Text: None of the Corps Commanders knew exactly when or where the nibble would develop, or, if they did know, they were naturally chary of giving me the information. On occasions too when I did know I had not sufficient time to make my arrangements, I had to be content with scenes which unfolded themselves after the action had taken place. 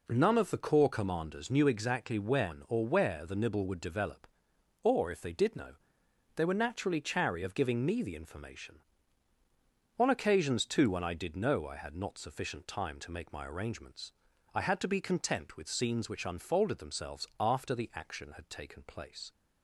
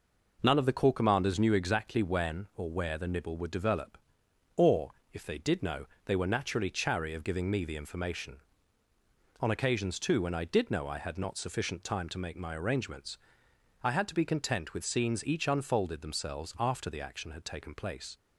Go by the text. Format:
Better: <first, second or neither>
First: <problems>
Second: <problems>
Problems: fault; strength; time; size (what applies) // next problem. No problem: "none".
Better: first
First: none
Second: says "each" for "which"; at 15.2 s